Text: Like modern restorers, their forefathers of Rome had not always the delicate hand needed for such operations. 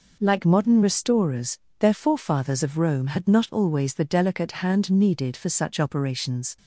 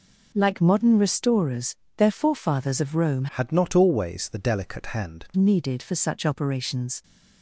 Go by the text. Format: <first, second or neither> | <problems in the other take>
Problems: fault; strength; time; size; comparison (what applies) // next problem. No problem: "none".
first | changes voice from "had" to "hand"; from 3.3 to 5.2 s; 1.9 s long